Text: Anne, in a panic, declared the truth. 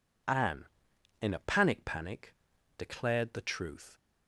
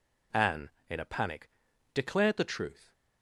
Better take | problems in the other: second | says "panic" twice; at 1.8 s

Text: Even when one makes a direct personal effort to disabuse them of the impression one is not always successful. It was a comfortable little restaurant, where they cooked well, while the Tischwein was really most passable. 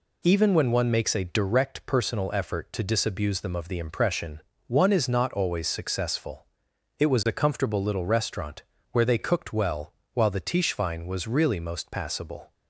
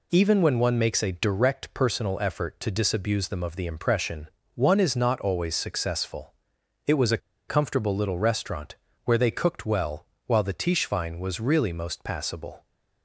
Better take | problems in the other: first | pauses between "impression" and "one"; slight; at 4.2 s; 0.26 s long; slight in the first // pauses between "a" and "comfortable"; slight; at 7.1 s; 0.30 s long

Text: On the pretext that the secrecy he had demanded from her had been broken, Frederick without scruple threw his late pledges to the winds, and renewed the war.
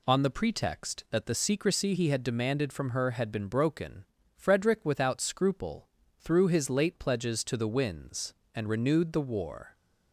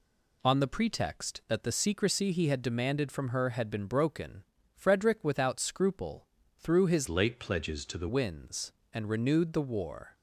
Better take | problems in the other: first | pauses between "scruple" and "threw"; slight; at 6.2 s; 0.28 s long; slight in the first // changes voice from "late" to "the"; from 7.0 to 8.0 s; 1.0 s long

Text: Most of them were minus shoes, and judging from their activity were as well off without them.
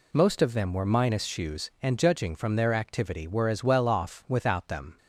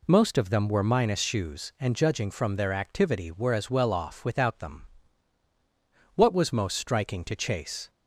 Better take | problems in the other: first | goes on to say "What was most striking to Chase"; strong; from 6.1 s on; 1.7 s long

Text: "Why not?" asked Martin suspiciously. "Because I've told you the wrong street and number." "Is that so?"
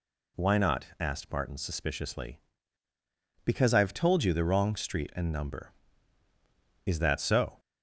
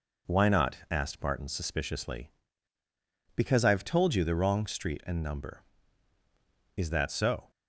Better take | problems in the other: first | gets quieter; throughout; 3.5 dB

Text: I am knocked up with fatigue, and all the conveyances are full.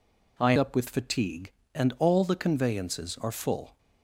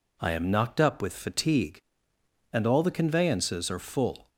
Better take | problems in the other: second | skips "am knocked"; at 0.5 s

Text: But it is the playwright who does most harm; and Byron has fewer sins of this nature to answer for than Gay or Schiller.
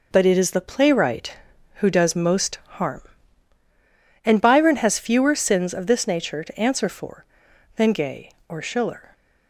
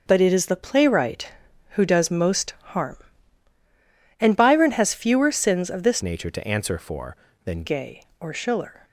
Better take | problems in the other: first | starts louder than the rest; noticeable; until 1.0 s; 6 dB // pauses between "most" and "harm"; slight; at 2.5 s; 0.18 s long; slight in the first // changes voice from "nature" to "than"; from 6.0 to 7.6 s; 1.6 s long

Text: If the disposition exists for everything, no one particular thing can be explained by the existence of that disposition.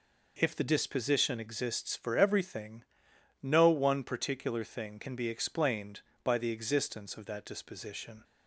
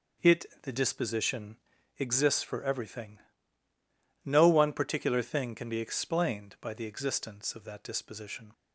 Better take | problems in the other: first | says "It" for "If"; at 0.2 s // pauses between "disposition" and "exists"; at 1.5 s; 0.38 s long

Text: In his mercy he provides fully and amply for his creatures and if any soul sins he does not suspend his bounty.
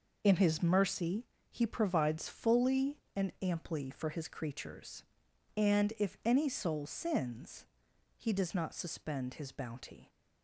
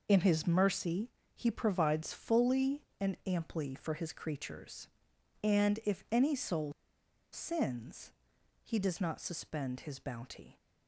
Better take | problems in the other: first | pauses between "mercy" and "he"; slight; at 1.0 s; 0.24 s long; slight in the first // pauses between "soul" and "sins"; noticeable; at 6.7 s; 0.61 s long // pauses between "sins" and "he"; noticeable; at 8.1 s; 0.52 s long; noticeable in the first

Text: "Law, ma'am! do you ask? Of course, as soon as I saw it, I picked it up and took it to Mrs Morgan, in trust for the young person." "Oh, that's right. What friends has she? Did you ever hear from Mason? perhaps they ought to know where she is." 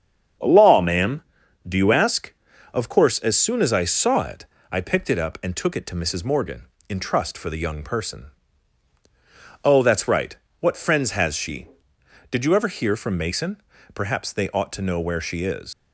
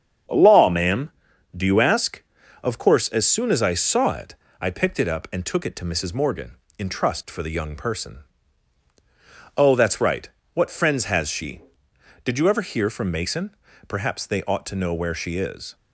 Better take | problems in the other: second | starts louder than the rest; strong; until 1.8 s; 7.5 dB; strong in the second // leaves "is" unfinished; at 15.7 s; 85 ms

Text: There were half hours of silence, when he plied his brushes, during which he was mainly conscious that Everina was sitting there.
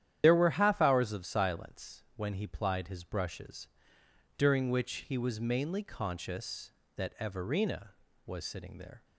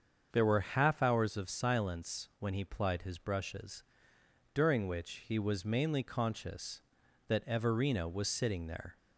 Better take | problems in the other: second | loses the start of "There"; at 0.2 s; 75 ms // starts louder than the rest; strong; until 1.2 s; 10.5 dB; also in the second

